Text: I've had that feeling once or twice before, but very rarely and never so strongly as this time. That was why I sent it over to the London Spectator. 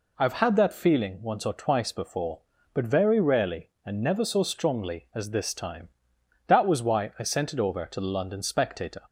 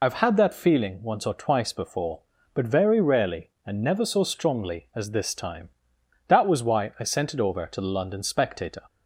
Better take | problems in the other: first | loses the start of "I've"; at 0.0 s; 50 ms

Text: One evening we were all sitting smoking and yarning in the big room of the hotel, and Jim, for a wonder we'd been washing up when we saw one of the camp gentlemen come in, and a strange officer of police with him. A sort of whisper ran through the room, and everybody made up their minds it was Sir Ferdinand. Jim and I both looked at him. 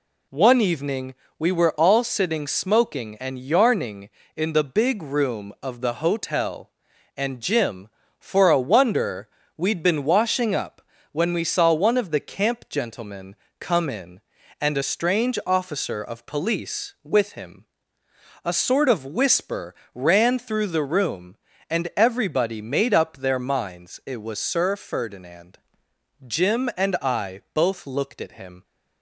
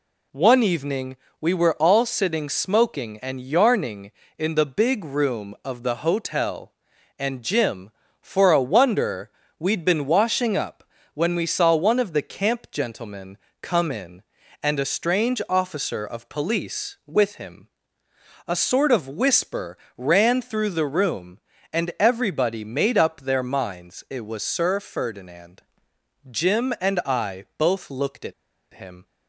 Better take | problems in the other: first | pauses between "evening" and "we"; slight; at 1.1 s; 0.24 s long; slight in the first // pauses between "wonder" and "we'd"; slight; at 9.2 s; 0.28 s long; slight in the first // pauses between "up" and "when"; slight; at 10.8 s; 0.30 s long; slight in the first // pauses between "gentlemen" and "come"; slight; at 13.3 s; 0.24 s long; slight in the first // pauses between "whisper" and "ran"; slight; at 19.7 s; 0.18 s long; slight in the first // pauses between "at" and "him"; at 28.3 s; 0.40 s long

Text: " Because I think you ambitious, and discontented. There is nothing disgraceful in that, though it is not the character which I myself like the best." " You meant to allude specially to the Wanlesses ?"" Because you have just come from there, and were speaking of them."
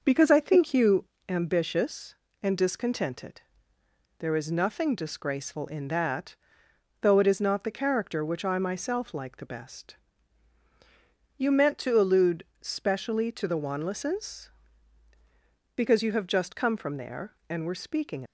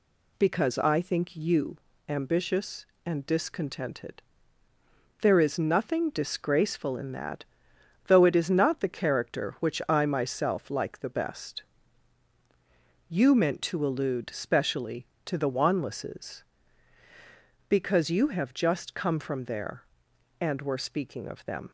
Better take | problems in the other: second | starts louder than the rest; noticeable; until 1.0 s; 6 dB // pauses between "you" and "ambitious"; slight; at 1.0 s; 0.22 s long; slight in the second // pauses between "allude" and "specially"; slight; at 12.4 s; 0.16 s long // stops before "of them"; at 18.2 s

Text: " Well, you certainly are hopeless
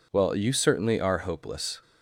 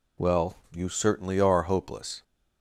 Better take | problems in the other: first | changes voice at "Well"; from 0.1 s on; 2.1 s long

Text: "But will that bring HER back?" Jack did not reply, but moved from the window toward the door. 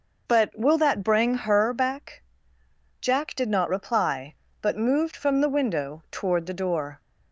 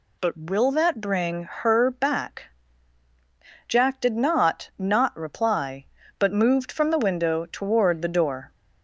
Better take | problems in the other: first | says "not" twice; at 4.7 s

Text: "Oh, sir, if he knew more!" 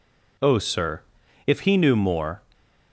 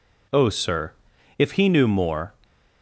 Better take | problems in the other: neither | stays silent after the last word; slight; the same in both

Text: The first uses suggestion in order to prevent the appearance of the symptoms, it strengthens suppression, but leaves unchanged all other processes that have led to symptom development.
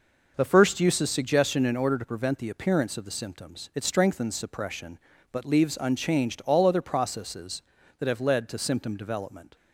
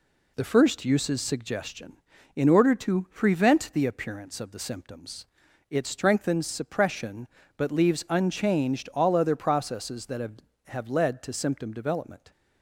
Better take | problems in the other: first | says "have" twice; at 10.6 s

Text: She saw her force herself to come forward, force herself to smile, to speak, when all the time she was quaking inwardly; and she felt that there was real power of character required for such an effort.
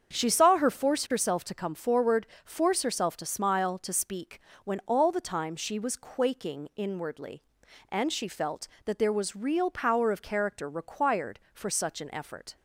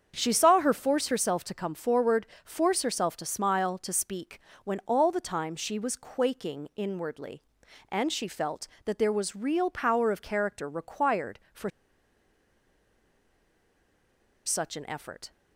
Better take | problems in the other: first | starts louder than the rest; strong; until 1.1 s; 7.5 dB; strong in the first // pauses between "for" and "such"; strong; at 11.6 s; 2.7 s long

